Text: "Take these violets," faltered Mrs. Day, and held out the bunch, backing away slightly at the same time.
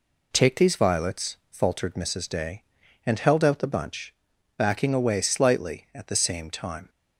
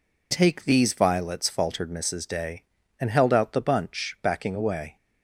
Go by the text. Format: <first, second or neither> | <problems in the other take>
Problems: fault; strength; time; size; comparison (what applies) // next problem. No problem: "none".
first | stops before "slightly at the same time"; at 4.9 s